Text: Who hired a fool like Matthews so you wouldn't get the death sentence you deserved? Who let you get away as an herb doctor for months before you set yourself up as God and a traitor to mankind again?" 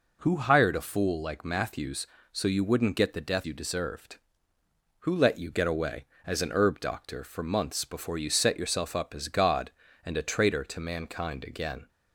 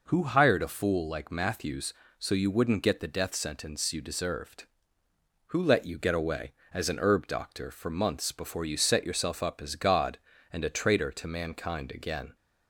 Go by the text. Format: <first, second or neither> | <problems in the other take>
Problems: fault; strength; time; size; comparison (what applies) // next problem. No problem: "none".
second | skips "sentence"; at 3.4 s